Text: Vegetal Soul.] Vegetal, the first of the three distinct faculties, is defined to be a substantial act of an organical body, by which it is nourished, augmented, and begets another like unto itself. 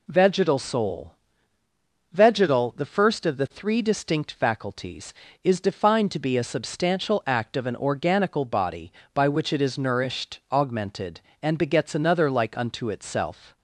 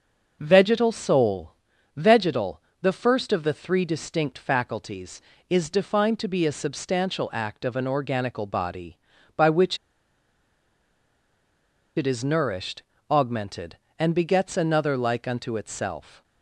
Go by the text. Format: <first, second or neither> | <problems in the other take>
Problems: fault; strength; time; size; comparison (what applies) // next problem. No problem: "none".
first | starts louder than the rest; until 1.4 s; 6 dB // pauses between "which" and "it"; strong; at 9.7 s; 2.1 s long